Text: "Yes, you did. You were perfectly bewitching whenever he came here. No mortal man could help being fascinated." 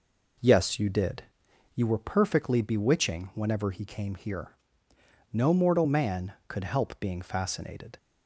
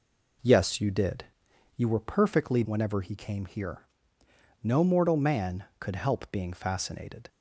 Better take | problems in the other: first | skips "bewitching"; at 2.6 s

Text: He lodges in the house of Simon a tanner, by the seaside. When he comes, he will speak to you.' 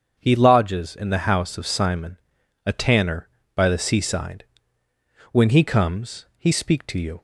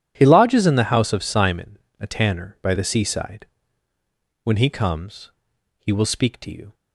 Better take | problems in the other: second | starts louder than the rest; until 1.2 s; 6.5 dB // pauses between "Simon" and "a"; noticeable; at 2.1 s; 0.48 s long; slight in the second // skips "will"; at 6.5 s

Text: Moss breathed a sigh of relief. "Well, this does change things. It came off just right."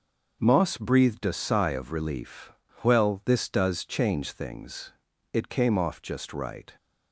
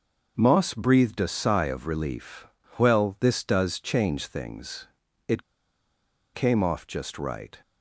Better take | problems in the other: first | starts louder than the rest; until 1.3 s; 6.5 dB; also in the first // pauses between "It" and "came"; noticeable; at 5.4 s; 0.90 s long

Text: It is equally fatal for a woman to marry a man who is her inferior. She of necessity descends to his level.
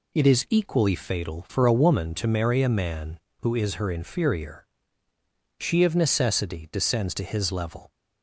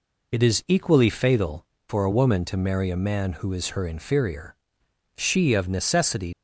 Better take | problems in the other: first | stops before "descends to his level"; at 6.3 s

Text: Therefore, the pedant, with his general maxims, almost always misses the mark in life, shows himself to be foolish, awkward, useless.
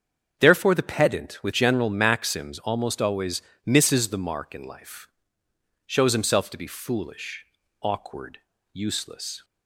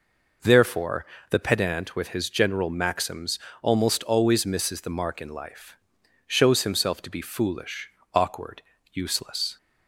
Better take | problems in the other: second | starts louder than the rest; strong; until 1.3 s; 7.5 dB // skips "his"; at 1.5 s // pauses between "always" and "misses"; slight; at 3.4 s; 0.24 s long

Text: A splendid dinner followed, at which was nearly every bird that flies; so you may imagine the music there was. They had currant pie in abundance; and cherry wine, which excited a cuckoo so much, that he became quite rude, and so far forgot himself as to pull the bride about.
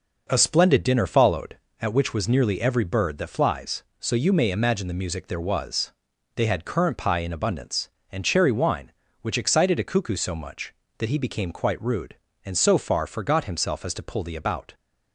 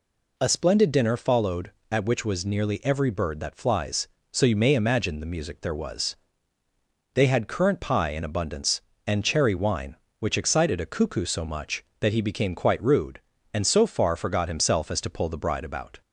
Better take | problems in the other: second | skips "bride"; at 14.3 s

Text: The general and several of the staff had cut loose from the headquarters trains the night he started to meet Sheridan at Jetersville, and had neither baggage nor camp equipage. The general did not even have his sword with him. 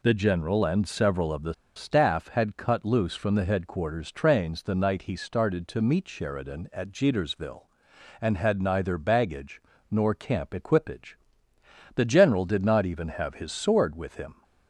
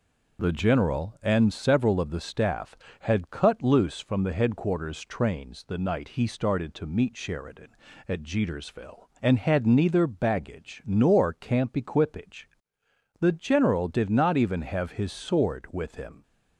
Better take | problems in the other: second | pauses between "the" and "staff"; slight; at 1.5 s; 0.22 s long // pauses between "baggage" and "nor"; slight; at 9.6 s; 0.28 s long

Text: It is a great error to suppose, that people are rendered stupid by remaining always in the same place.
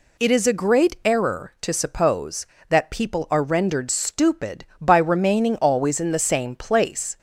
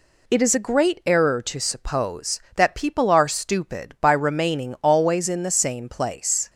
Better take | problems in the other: first | skips "rendered"; at 3.2 s

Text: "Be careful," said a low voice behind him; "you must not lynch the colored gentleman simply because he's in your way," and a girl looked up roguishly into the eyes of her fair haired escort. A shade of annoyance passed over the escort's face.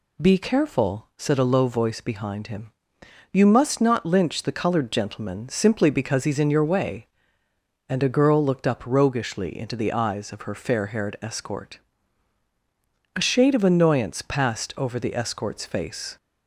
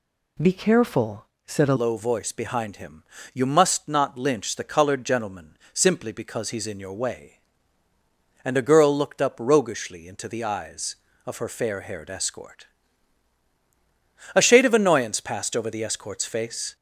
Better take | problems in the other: first | changes voice at "low"; from 1.7 s on; 15.0 s long // pauses between "gentleman" and "simply"; slight; at 5.5 s; 0.16 s long

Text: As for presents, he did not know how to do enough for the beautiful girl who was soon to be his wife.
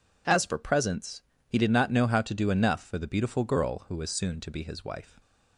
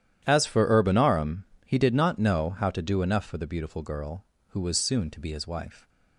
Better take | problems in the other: first | starts louder than the rest; strong; until 1.2 s; 10.5 dB // says "urbanarum" for "presents"; at 0.6 s

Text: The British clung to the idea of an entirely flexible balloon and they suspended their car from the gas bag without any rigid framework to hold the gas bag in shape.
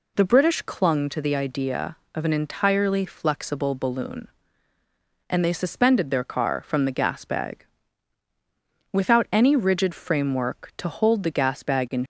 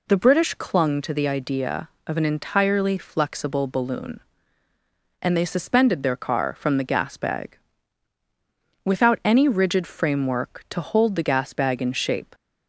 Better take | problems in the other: second | pauses between "bag" and "without"; strong; at 7.6 s; 1.2 s long; strong in the second // stops before "shape"; at 12.0 s

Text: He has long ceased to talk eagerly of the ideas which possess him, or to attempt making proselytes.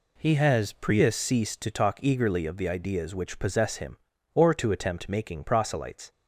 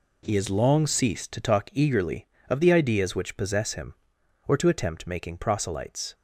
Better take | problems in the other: second | says "prius" for "long"; at 0.7 s

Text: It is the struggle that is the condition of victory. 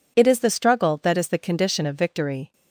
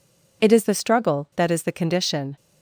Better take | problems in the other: first | stops before "of victory"; at 2.3 s

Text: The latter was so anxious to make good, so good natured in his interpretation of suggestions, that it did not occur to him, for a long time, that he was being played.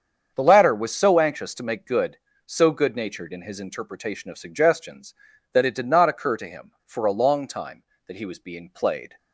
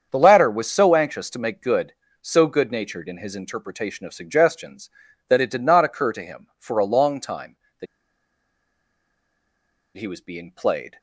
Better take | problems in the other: first | starts louder than the rest; strong; until 1.1 s; 7.5 dB; strong in the first // pauses between "that" and "he"; strong; at 7.8 s; 2.1 s long

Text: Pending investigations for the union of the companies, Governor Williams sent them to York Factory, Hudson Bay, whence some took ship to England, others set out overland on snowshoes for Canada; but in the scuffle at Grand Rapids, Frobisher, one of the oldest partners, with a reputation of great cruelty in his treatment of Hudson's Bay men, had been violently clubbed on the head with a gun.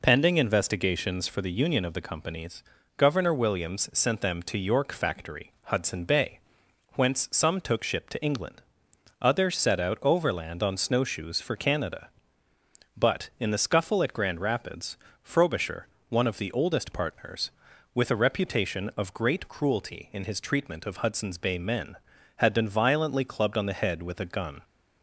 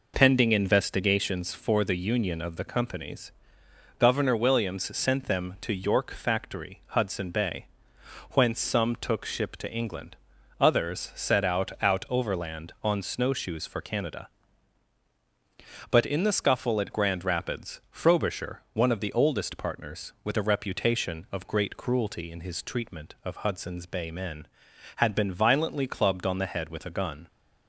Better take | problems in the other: first | says "out" twice; at 11.8 s

